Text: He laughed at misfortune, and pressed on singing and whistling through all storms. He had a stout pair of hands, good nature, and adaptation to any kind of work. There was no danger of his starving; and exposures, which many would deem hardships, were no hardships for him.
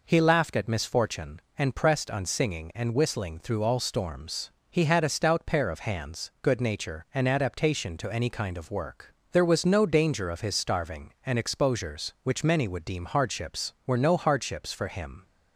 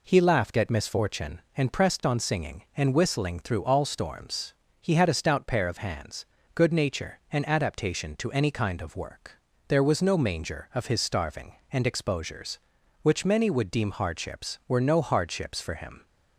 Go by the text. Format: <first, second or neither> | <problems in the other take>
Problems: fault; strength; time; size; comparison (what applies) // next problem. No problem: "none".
first | says "manger" for "danger"; at 10.1 s